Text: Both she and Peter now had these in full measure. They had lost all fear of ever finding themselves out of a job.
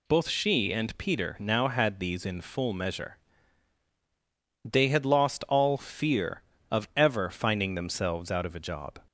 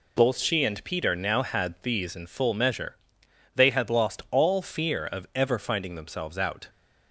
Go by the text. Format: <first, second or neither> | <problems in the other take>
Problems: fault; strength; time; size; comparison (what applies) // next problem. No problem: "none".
first | stops before "of a job"; at 6.6 s